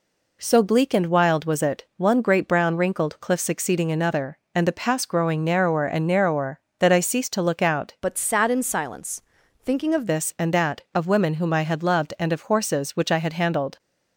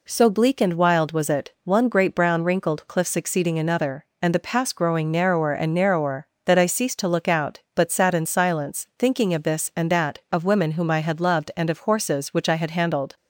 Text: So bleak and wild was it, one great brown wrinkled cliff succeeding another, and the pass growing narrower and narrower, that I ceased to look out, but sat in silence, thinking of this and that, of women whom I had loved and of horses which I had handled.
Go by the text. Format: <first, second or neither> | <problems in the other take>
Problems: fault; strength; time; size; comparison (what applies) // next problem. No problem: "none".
second | changes voice from "but" to "of"; from 8.0 to 10.0 s; 2.0 s long